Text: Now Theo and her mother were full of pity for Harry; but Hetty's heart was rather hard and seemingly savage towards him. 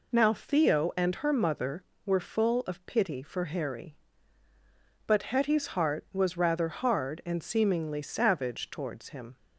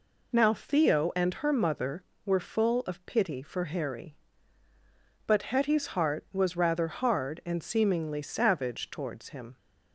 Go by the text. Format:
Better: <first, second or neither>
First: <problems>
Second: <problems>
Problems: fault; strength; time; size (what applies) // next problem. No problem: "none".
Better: neither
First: none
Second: none